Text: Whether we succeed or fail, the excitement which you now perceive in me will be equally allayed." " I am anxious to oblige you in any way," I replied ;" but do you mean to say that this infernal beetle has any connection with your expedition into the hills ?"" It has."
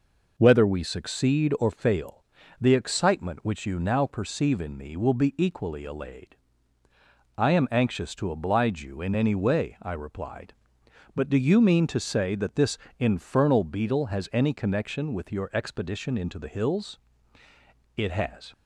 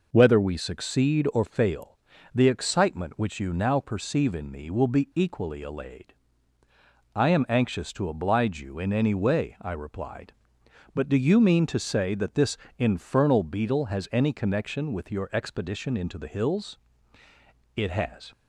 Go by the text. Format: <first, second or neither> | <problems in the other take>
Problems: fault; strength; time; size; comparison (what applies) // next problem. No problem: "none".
neither | pauses between "this" and "infernal"; slight; the same in both